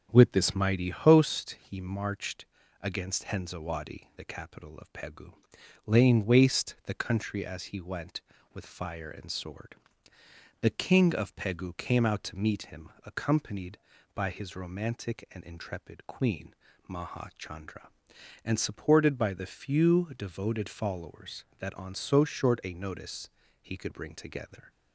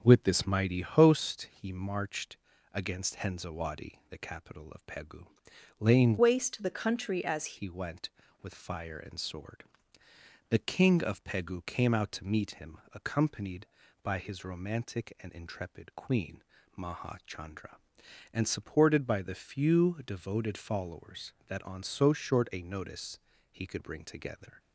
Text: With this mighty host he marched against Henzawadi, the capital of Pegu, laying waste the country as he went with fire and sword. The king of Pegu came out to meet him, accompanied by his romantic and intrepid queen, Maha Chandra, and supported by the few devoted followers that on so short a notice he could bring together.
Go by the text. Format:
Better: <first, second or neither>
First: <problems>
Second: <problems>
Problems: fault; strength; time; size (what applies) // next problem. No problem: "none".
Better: first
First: starts louder than the rest; strong; until 1.1 s; 7.5 dB // pauses between "marched" and "against"; slight; at 2.4 s; 0.34 s long // pauses between "notice" and "he"; slight; at 23.2 s; 0.32 s long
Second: starts louder than the rest; until 1.0 s; 7 dB // pauses between "marched" and "against"; slight; at 2.3 s; 0.34 s long // changes voice from "waste" to "as"; from 6.1 to 7.5 s; 1.4 s long // pauses between "notice" and "he"; slight; at 23.1 s; 0.32 s long